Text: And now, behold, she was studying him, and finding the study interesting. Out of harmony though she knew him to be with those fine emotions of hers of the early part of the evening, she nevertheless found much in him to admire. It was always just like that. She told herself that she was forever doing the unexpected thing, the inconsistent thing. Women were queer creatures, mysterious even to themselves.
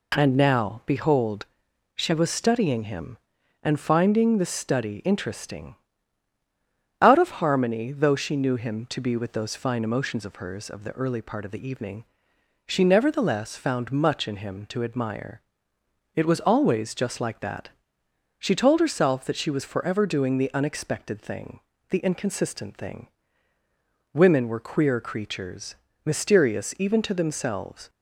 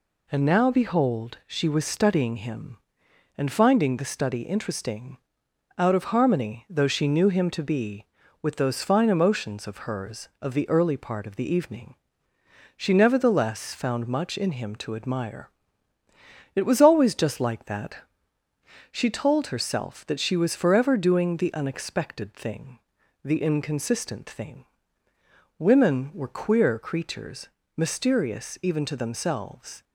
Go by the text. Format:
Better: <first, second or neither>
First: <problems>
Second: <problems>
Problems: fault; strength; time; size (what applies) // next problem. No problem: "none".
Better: neither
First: none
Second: none